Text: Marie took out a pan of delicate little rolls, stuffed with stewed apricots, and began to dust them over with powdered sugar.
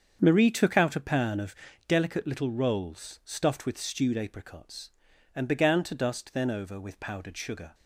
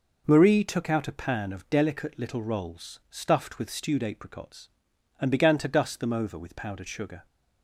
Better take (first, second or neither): second